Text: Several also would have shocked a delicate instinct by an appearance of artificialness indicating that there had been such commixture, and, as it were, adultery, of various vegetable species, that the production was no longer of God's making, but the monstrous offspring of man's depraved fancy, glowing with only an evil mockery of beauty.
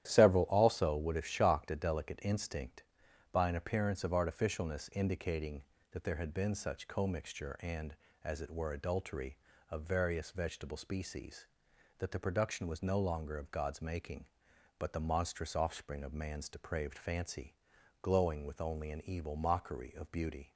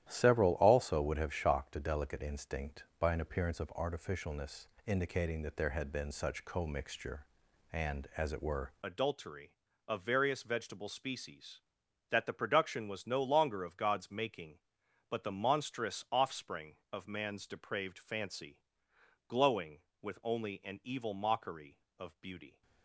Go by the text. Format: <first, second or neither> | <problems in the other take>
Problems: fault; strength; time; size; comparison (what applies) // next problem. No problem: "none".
first | starts louder than the rest; strong; until 1.1 s; 11.5 dB; strong in the first // pauses between "artificialness" and "indicating"; slight; at 4.6 s; 0.18 s long // changes voice at "adultery"; from 8.8 s on; 13.8 s long